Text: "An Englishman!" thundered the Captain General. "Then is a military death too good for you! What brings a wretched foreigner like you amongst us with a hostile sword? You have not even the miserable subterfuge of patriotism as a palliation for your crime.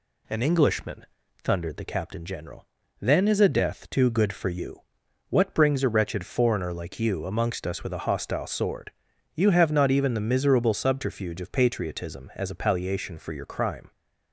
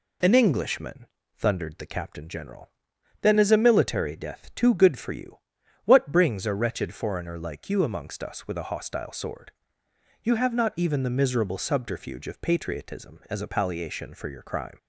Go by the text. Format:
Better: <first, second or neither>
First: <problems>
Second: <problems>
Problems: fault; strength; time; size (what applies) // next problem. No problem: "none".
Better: second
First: skips "military"; at 3.4 s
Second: none